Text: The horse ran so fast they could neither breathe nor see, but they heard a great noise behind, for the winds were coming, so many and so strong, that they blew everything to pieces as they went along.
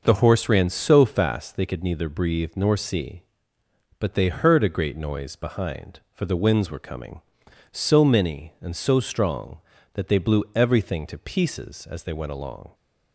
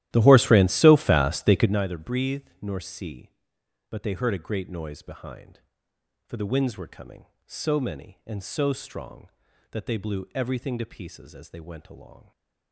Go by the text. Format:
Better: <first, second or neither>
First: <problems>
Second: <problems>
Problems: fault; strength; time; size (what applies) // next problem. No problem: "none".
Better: first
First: none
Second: starts louder than the rest; strong; until 1.8 s; 14 dB